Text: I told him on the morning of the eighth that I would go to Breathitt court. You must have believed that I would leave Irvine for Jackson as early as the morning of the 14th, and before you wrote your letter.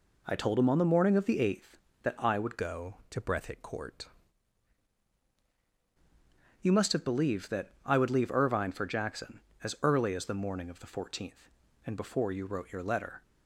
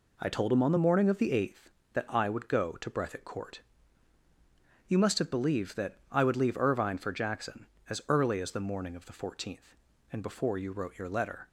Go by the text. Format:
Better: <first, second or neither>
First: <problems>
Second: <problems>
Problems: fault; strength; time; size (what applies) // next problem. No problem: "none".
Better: second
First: changes voice from "go" to "court"; from 2.5 to 4.0 s; 1.5 s long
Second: none